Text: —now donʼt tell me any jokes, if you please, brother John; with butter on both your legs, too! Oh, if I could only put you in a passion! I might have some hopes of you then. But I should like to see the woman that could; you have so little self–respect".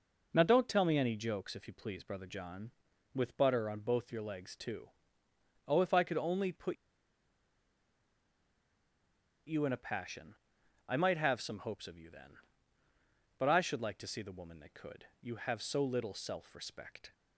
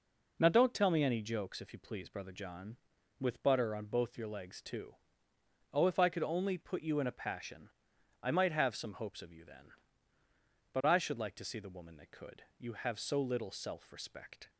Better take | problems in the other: second | pauses between "put" and "you"; strong; at 6.7 s; 2.7 s long

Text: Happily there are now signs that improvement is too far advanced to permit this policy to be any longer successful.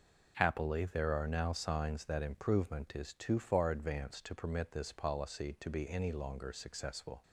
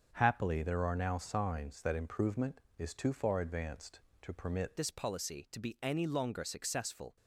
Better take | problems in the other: first | starts louder than the rest; until 1.1 s; 7 dB // changes voice at "this"; from 4.7 s on; 2.4 s long

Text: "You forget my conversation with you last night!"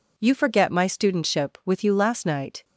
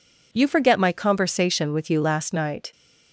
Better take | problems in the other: second | says "studentship" for "conversation"; at 0.8 s

